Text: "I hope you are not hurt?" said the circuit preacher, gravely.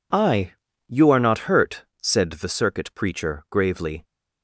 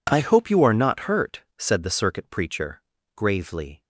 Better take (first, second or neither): second